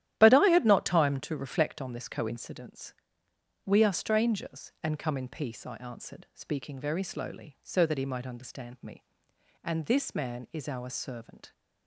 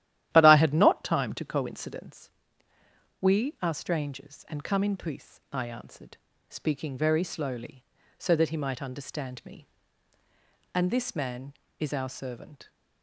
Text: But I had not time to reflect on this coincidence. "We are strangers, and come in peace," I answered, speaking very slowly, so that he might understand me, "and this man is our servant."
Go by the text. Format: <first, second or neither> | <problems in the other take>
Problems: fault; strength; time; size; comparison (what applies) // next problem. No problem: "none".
first | starts louder than the rest; strong; until 1.3 s; 13 dB; strong in the first // skips "reflect on this"; at 1.4 s